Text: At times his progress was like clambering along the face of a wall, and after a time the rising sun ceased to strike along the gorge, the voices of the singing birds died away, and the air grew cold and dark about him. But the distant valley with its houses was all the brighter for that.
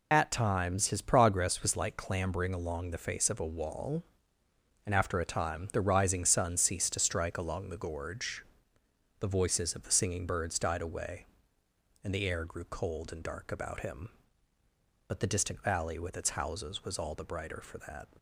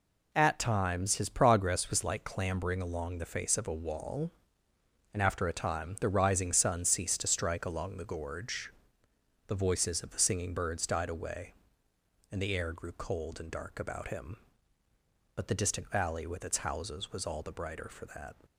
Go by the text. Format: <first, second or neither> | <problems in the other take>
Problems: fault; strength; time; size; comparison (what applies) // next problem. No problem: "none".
second | loses the start of "At"; at 0.1 s; 50 ms